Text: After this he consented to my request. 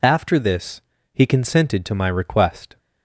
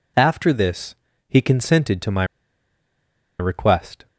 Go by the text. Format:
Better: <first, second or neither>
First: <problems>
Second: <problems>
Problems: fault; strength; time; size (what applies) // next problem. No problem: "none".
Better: first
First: pauses between "this" and "he"; slight; at 0.8 s; 0.33 s long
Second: pauses between "this" and "he"; slight; at 0.9 s; 0.34 s long // pauses between "my" and "request"; at 2.2 s; 1.1 s long